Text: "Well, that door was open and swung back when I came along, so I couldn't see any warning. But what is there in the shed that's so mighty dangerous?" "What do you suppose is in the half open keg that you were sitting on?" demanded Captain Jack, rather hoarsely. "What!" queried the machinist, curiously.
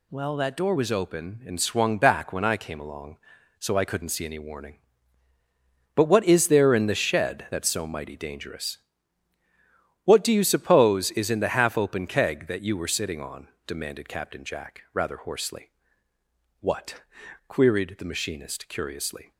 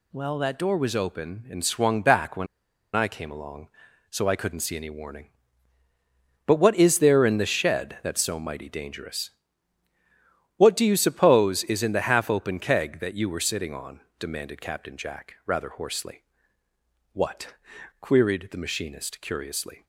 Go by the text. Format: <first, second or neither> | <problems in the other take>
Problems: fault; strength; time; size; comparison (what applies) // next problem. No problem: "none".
first | pauses between "when" and "I"; noticeable; at 2.4 s; 0.49 s long